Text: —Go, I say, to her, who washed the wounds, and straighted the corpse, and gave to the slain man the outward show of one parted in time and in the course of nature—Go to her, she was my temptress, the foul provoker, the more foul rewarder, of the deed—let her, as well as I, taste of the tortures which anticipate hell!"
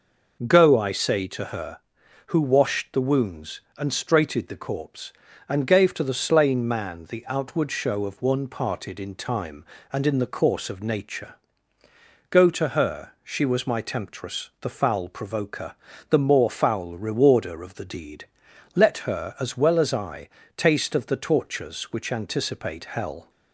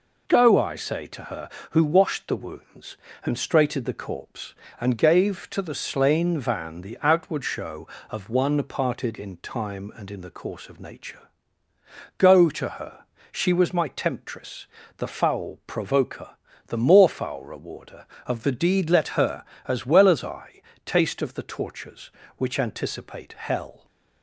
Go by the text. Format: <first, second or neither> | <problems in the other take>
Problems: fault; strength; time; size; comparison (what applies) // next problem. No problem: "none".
first | says "van" for "man"; at 6.3 s